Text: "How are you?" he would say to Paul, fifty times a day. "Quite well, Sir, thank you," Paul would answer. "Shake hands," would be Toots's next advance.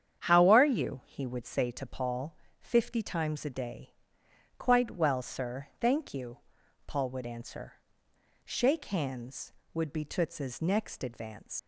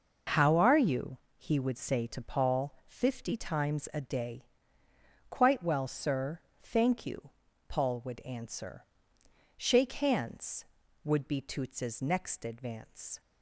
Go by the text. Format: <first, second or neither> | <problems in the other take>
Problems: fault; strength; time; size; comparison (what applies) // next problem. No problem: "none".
second | starts louder than the rest; strong; until 1.2 s; 8.5 dB // leaves "advance" unfinished; at 11.5 s; 105 ms